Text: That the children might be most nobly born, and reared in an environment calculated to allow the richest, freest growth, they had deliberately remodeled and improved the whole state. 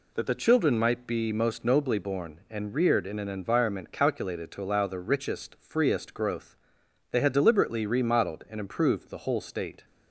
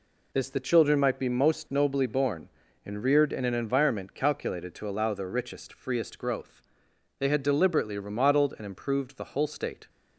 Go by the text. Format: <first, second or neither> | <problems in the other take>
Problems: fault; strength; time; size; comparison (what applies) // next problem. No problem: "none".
first | says "This" for "That"; at 0.3 s